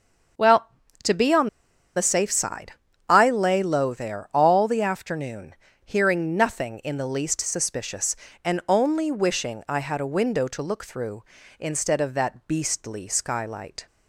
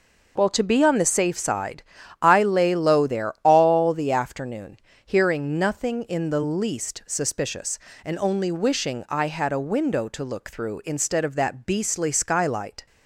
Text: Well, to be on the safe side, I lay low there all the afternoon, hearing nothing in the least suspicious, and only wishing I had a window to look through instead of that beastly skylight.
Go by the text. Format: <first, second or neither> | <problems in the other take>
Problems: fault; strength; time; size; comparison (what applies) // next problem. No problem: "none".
second | starts louder than the rest; until 2.2 s; 6.5 dB // pauses between "on" and "the"; noticeable; at 1.4 s; 0.48 s long